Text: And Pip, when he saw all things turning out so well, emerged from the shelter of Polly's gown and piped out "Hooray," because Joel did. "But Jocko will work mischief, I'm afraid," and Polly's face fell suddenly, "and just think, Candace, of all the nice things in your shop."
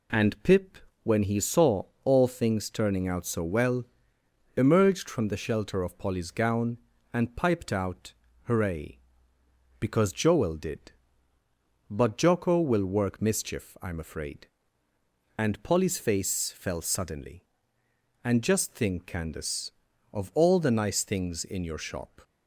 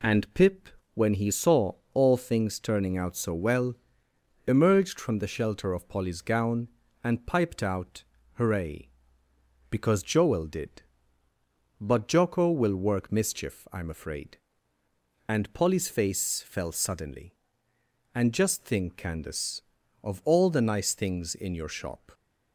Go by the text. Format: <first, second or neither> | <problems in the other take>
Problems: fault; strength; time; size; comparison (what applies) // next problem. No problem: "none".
neither | pauses between "saw" and "all"; slight; the same in both // pauses between "out" and "Hooray"; slight; the same in both